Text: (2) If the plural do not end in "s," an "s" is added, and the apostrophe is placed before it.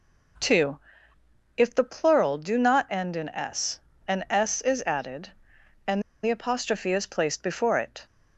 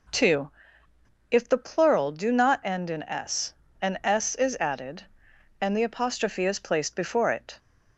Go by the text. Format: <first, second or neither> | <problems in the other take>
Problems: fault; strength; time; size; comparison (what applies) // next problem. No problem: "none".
second | pauses between "and" and "the"; slight; at 6.0 s; 0.21 s long